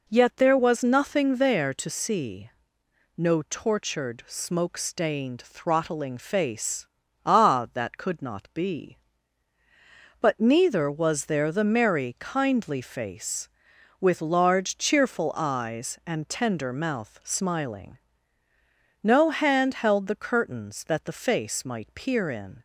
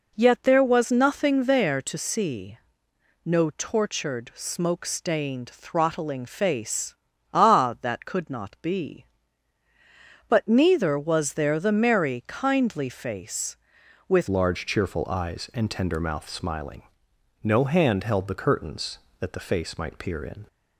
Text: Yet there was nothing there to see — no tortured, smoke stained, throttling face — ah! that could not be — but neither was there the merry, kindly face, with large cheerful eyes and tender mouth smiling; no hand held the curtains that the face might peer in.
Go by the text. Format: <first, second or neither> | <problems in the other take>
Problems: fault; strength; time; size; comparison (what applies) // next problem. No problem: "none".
first | changes voice at "large"; from 14.2 s on; 6.2 s long